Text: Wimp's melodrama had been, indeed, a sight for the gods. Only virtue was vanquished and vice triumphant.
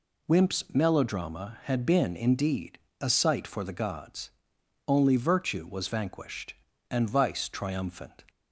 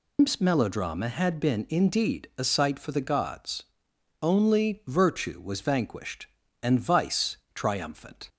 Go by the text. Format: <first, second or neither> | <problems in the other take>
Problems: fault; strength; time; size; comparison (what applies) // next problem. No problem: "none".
first | loses the start of "Wimp's"; at 0.1 s; 160 ms // pauses between "vice" and "triumphant"; slight; at 7.3 s; 0.16 s long